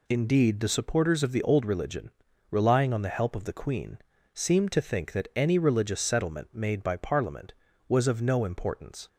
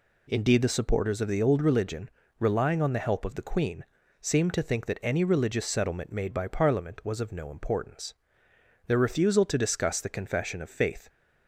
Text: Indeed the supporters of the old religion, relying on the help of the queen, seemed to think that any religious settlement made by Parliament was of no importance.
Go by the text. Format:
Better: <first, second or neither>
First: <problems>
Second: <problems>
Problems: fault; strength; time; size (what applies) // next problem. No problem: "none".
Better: first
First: none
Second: goes on to say "Their refusal to discuss the confession of faith"; strong; from 8.8 s on; 2.2 s long